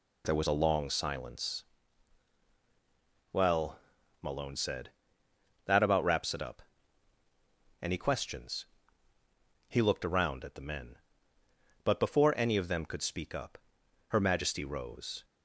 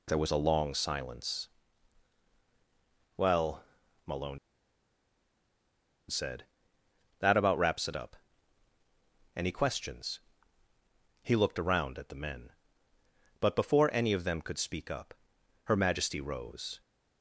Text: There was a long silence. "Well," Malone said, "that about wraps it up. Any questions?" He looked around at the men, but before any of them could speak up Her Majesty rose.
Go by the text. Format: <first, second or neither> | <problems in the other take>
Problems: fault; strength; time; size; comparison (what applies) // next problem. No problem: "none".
first | pauses between "Malone" and "said"; strong; at 4.3 s; 1.7 s long // pauses between "up" and "Her"; noticeable; at 15.1 s; 0.52 s long; noticeable in the first